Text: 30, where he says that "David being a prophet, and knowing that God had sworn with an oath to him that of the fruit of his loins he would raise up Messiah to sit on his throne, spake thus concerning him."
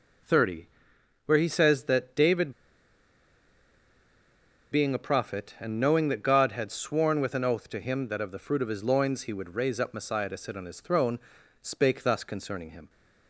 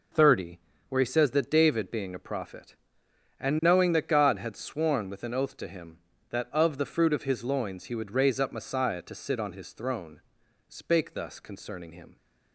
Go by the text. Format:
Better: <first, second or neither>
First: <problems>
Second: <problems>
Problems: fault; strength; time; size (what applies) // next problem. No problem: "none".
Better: second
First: pauses between "David" and "being"; strong; at 2.5 s; 2.1 s long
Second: none